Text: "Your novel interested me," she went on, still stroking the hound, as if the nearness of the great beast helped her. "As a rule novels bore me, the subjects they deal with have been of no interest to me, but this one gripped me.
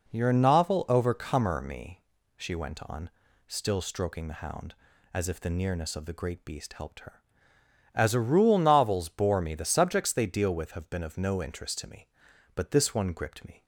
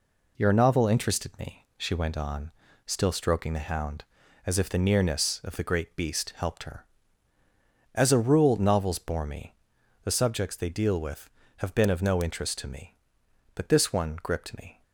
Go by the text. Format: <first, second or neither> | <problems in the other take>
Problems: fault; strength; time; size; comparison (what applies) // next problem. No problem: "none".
second | says "overcomer" for "interested"; at 0.8 s